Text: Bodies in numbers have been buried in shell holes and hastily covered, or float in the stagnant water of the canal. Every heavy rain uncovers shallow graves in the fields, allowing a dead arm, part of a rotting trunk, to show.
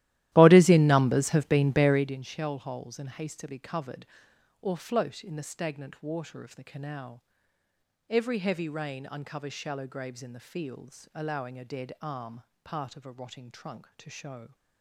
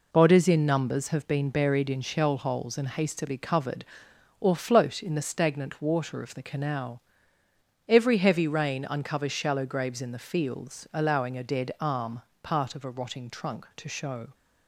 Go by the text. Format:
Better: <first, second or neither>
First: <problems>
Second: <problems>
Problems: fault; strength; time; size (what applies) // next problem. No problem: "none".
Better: second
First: starts louder than the rest; strong; until 2.2 s; 15 dB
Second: none